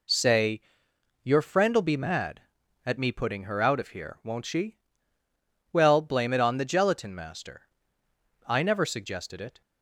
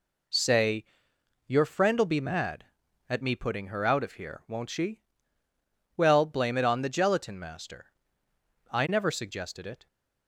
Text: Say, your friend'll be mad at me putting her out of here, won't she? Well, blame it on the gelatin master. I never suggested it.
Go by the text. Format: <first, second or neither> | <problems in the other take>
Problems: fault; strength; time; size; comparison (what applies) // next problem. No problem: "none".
neither | none